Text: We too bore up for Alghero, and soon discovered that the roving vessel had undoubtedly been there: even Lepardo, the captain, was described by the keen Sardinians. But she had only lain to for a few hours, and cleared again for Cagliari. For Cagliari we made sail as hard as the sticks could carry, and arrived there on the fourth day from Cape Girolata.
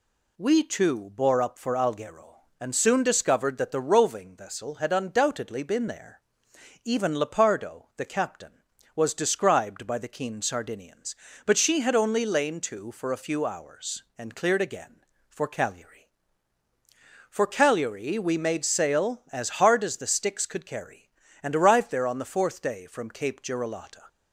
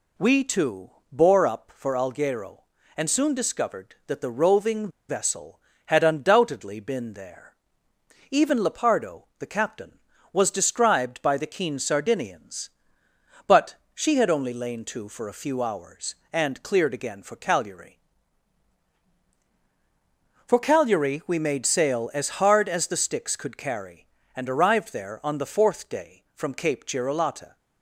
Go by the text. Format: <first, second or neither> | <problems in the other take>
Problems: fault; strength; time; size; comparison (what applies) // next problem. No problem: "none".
first | pauses between "too" and "bore"; slight; at 0.9 s; 0.20 s long // pauses between "roving" and "vessel"; slight; at 4.8 s; 0.20 s long // pauses between "But" and "she"; slight; at 13.7 s; 0.20 s long